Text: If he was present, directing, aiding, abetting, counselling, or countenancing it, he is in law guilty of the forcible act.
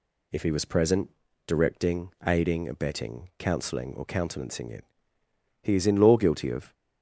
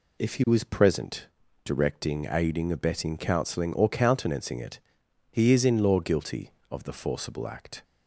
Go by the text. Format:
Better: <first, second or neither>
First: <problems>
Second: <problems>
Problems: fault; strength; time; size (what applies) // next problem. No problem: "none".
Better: second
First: stops before "the forcible act"; at 6.7 s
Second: none